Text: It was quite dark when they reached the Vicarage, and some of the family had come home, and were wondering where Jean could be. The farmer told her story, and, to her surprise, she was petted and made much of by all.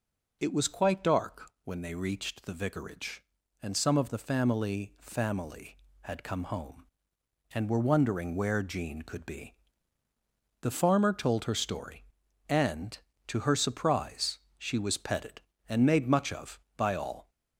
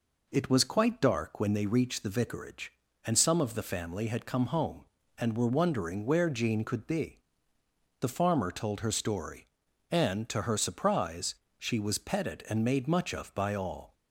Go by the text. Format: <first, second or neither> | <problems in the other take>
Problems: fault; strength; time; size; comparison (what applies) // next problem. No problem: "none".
second | says "family" twice; at 4.9 s